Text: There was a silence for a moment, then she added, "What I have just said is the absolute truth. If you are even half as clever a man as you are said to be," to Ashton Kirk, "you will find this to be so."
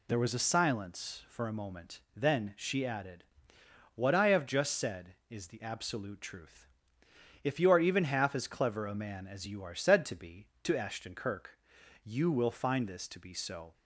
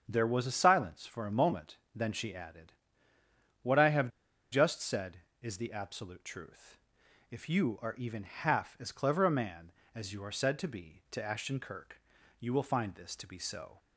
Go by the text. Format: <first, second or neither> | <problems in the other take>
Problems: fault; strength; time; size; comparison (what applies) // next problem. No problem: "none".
first | starts louder than the rest; strong; until 1.0 s; 8 dB // pauses between "have" and "just"; at 4.0 s; 0.44 s long